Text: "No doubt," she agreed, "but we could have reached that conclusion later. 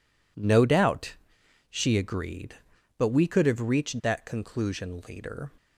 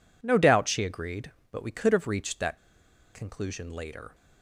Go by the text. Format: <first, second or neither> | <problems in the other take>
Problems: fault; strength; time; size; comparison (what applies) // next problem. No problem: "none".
first | pauses between "that" and "conclusion"; noticeable; at 2.5 s; 0.57 s long